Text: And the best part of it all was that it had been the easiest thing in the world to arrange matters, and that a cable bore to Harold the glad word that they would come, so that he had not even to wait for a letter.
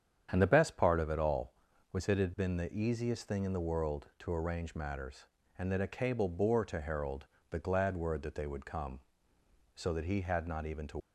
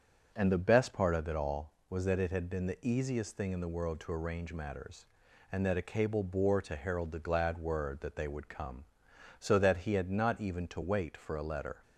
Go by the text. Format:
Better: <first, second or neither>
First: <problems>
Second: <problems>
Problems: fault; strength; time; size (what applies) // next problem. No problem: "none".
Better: second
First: starts louder than the rest; strong; until 1.3 s; 8.5 dB // pauses between "Harold" and "the"; slight; at 7.2 s; 0.24 s long // stops before "wait for a letter"; at 10.9 s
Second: starts louder than the rest; until 1.3 s; 6.5 dB